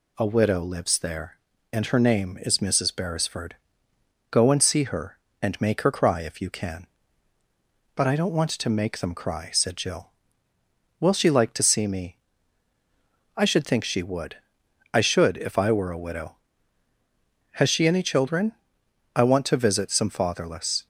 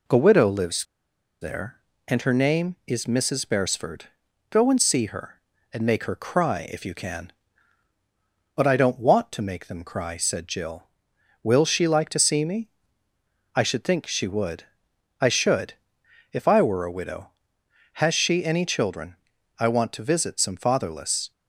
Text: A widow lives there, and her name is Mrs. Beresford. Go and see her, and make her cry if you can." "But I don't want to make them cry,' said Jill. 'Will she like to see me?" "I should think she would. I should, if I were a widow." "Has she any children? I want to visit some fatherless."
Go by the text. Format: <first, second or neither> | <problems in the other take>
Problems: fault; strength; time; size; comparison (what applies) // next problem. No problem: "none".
first | pauses between "lives" and "there"; noticeable; at 0.8 s; 0.57 s long